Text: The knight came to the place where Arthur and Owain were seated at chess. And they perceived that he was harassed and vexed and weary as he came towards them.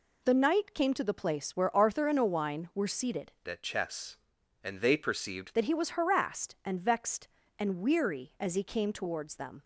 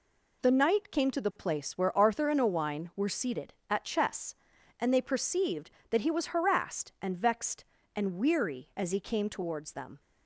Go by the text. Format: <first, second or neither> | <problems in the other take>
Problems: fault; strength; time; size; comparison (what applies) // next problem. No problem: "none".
second | changes voice from "at" to "perceived"; from 3.4 to 5.5 s; 2.1 s long